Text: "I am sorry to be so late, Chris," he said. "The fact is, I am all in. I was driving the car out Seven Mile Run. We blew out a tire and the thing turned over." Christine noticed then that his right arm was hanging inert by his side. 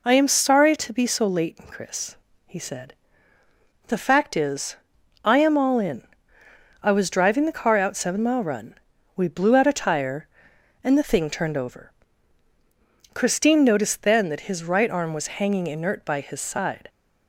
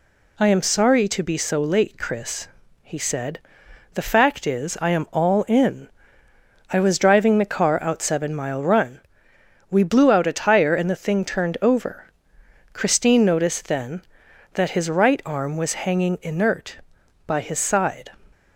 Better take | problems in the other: neither | none

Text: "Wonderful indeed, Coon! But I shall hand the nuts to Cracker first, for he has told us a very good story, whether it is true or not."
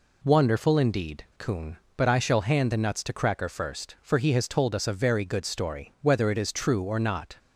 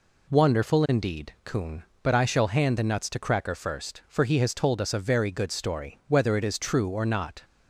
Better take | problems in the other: neither | none

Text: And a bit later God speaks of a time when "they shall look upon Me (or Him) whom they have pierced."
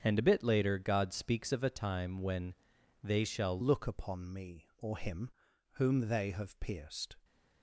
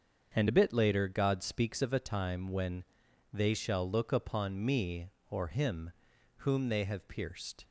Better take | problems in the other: second | starts louder than the rest; strong; until 1.0 s; 7.5 dB; also in the second // pauses between "when" and "they"; noticeable; at 2.5 s; 0.48 s long; noticeable in the second // changes voice at "look"; from 3.6 s on; 3.5 s long

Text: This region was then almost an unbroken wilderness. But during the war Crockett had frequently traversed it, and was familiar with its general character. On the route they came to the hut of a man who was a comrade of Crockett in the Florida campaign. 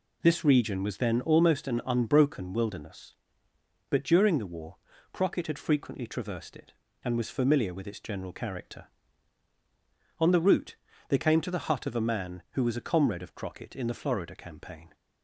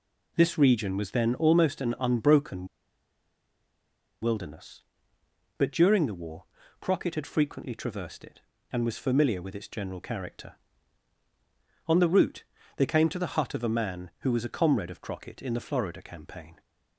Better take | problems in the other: first | pauses between "unbroken" and "wilderness"; strong; at 2.6 s; 1.5 s long // pauses between "war" and "Crockett"; slight; at 6.4 s; 0.36 s long; slight in the first // pauses between "route" and "they"; slight; at 12.4 s; 0.32 s long; slight in the first

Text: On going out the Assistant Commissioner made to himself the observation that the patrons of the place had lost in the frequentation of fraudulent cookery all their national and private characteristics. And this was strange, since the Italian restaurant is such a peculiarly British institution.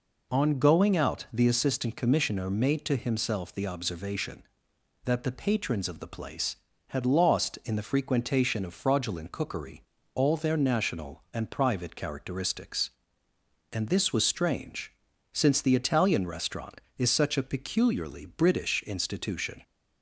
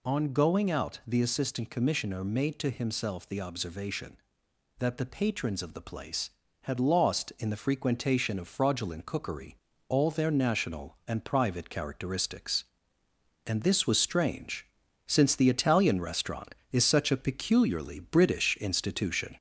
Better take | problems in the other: first | gets louder; slight; throughout; 2 dB // pauses between "cookery" and "all"; slight; at 9.5 s; 0.32 s long; slight in the first

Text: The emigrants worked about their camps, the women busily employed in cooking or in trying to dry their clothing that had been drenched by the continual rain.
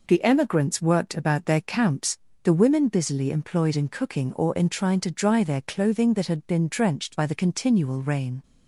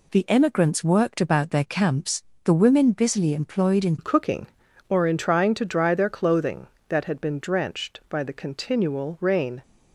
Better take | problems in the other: first | changes voice at "cooking"; from 3.9 s on; 5.7 s long

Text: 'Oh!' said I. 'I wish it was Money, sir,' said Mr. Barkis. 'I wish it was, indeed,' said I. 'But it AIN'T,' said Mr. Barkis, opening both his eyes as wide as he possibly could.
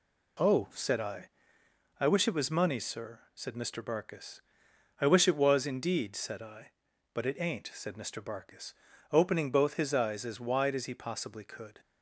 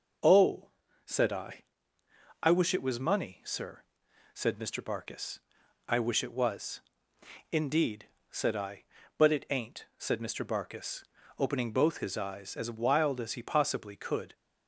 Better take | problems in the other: first | says "wild" for "wide"; at 12.6 s

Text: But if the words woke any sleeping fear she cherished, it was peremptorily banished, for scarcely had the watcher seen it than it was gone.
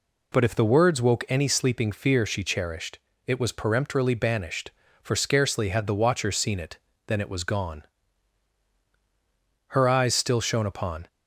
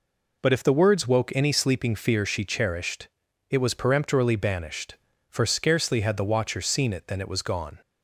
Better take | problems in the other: second | goes on to say "Her eyes still shone upon"; from 9.6 s on; 1.4 s long

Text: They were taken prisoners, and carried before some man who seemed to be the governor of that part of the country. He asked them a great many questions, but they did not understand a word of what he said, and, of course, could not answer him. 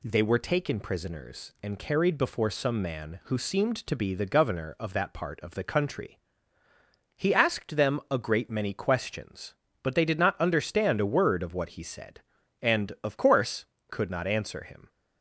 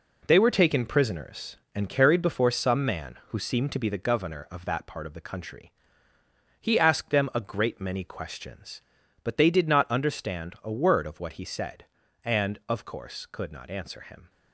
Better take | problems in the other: first | gets quieter; strong; throughout; 7.5 dB

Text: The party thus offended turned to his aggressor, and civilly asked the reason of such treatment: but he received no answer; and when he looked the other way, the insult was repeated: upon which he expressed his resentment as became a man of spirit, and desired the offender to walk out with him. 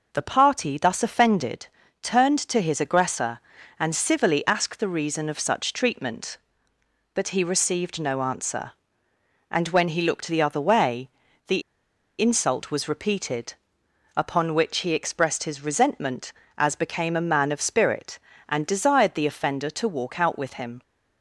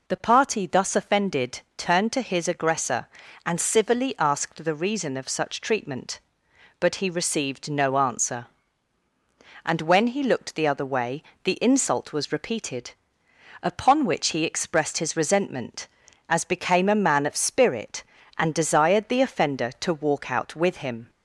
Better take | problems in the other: second | pauses between "offended" and "turned"; slight; at 1.6 s; 0.34 s long; slight in the second // pauses between "the" and "insult"; noticeable; at 11.6 s; 0.57 s long

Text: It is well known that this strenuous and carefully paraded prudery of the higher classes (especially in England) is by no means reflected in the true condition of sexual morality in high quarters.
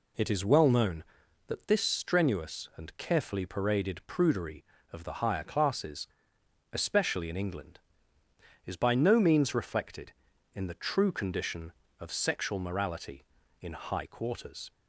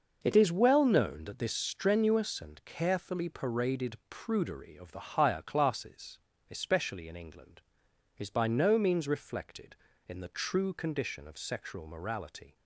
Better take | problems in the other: first | stops before "in high quarters"; at 12.5 s

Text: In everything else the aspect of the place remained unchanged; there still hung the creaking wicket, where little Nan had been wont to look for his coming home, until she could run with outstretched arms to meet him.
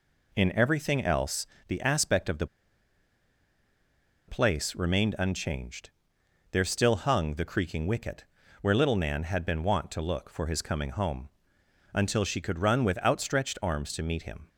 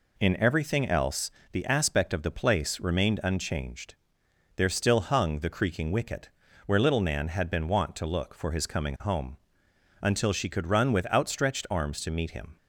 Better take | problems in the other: second | pauses between "else" and "the"; slight; at 1.4 s; 0.22 s long; slight in the second // pauses between "the" and "place"; strong; at 2.4 s; 1.8 s long

